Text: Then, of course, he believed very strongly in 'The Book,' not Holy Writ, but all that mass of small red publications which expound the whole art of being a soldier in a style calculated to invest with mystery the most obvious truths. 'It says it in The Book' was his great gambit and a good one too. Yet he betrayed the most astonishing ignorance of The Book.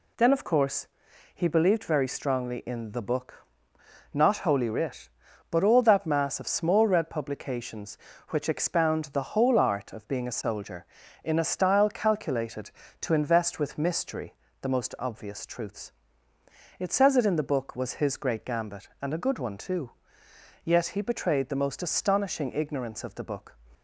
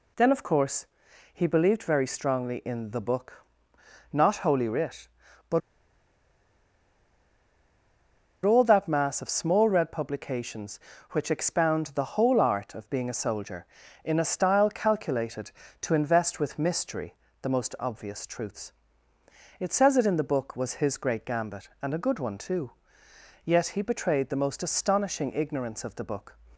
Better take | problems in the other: first | pauses between "but" and "all"; strong; at 5.6 s; 2.8 s long // pauses between "mystery" and "the"; slight; at 17.1 s; 0.28 s long; slight in the first

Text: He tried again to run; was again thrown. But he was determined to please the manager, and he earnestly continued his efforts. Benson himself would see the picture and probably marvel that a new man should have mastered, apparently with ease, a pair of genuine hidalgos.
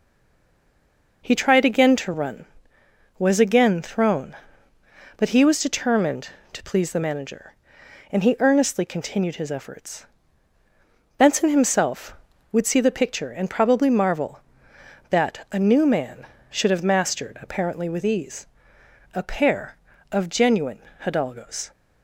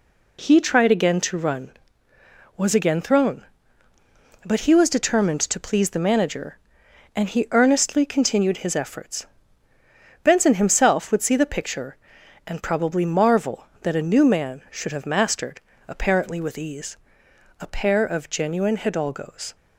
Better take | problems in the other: second | stays silent before the first word; noticeable; until 1.2 s; 1.2 s long // pauses between "genuine" and "hidalgos"; slight; at 20.8 s; 0.20 s long

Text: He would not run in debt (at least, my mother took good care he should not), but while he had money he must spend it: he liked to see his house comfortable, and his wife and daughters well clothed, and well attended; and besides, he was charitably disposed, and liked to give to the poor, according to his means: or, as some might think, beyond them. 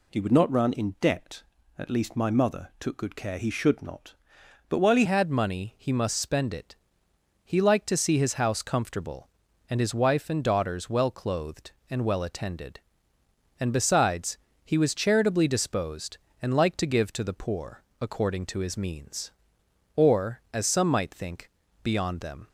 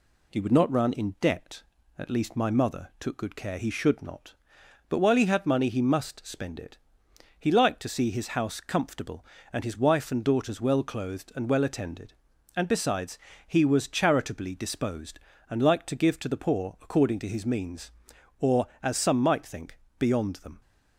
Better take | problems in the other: second | changes voice at "had"; from 5.0 s on; 17.4 s long

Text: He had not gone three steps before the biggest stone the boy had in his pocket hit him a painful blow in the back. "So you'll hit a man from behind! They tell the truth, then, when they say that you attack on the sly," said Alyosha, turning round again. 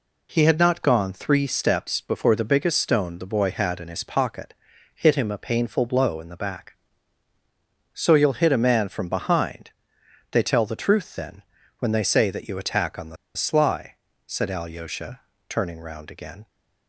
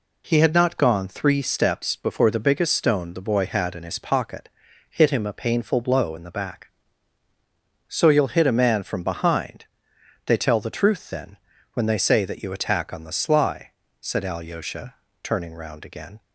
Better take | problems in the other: second | pauses between "pocket" and "hit"; at 4.5 s; 0.40 s long; also in the second // pauses between "the" and "sly"; slight; at 13.1 s; 0.20 s long

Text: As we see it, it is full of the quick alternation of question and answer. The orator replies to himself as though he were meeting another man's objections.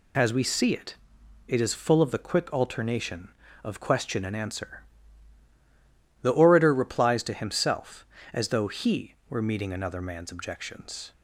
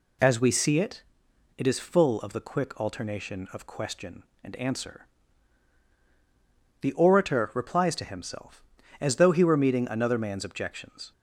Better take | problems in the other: neither | none

